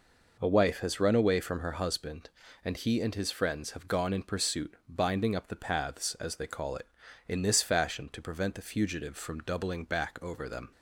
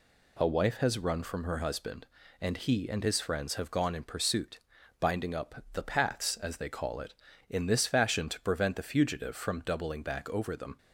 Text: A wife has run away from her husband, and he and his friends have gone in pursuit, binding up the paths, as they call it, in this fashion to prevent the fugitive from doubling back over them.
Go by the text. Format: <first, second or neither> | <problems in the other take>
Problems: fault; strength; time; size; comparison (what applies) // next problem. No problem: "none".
first | skips "away"; at 1.2 s